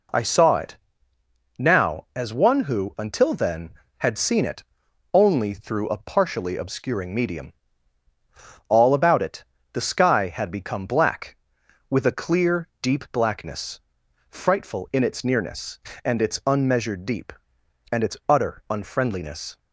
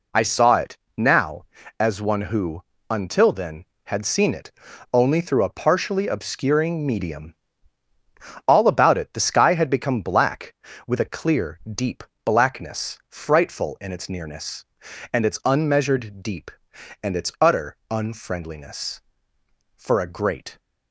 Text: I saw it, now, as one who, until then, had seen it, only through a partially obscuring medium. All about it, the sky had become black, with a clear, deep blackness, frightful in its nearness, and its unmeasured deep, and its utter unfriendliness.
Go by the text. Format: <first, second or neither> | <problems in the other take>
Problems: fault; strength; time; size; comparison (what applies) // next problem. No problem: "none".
first | pauses between "deep" and "blackness"; slight; at 12.0 s; 0.22 s long // goes on to say "For a great"; noticeable; from 19.7 s on; 0.82 s long